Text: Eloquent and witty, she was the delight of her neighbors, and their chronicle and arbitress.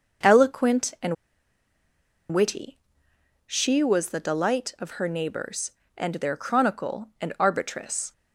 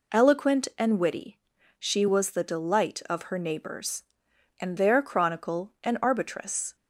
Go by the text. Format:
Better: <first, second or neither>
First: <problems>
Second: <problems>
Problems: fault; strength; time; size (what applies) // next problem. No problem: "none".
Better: second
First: starts louder than the rest; noticeable; until 2.4 s; 6 dB // pauses between "and" and "witty"; at 1.1 s; 1.1 s long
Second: none